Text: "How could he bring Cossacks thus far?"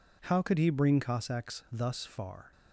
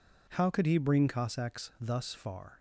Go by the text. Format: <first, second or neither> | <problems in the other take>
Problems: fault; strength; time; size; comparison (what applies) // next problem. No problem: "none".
neither | none